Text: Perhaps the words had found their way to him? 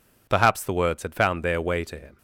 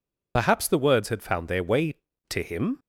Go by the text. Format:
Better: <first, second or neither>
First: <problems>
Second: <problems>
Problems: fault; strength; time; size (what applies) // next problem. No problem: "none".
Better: first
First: none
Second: loses the start of "Perhaps"; at 0.3 s; 55 ms